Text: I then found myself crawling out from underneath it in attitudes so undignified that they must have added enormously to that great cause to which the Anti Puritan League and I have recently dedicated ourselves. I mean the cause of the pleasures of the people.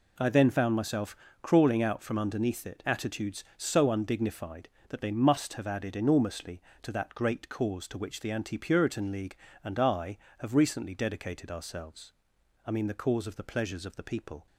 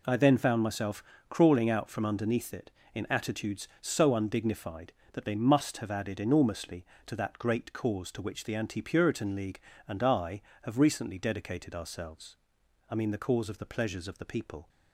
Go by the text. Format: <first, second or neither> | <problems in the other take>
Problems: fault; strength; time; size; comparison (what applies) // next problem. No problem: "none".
second | pauses between "myself" and "crawling"; slight; at 1.1 s; 0.26 s long; slight in the second // skips "in"; at 2.8 s